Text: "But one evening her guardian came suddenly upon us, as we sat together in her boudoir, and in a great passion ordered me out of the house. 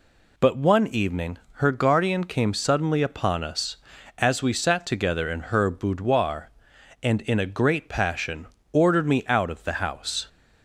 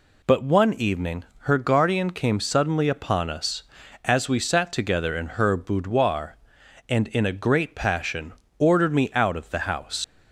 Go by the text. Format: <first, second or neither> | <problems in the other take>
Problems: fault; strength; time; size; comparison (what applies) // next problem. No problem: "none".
first | pauses between "evening" and "her"; slight; at 1.2 s; 0.24 s long; slight in the first // pauses between "passion" and "ordered"; slight; at 8.3 s; 0.28 s long; slight in the first // leaves "house" unfinished; at 10.0 s; 100 ms